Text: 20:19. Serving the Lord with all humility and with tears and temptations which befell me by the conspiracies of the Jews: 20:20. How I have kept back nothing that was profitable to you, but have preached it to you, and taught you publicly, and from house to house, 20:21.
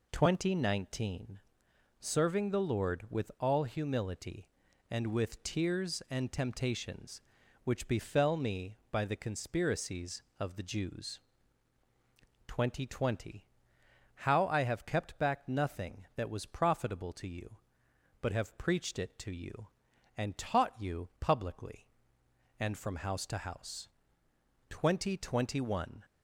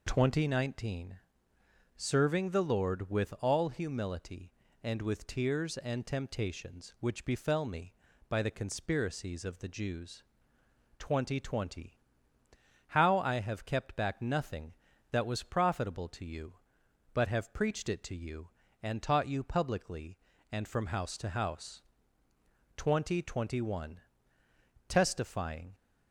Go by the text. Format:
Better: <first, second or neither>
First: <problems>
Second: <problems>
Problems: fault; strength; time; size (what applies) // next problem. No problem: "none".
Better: first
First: none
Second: goes on to say "Testifying"; noticeable; from 24.8 s on; 0.86 s long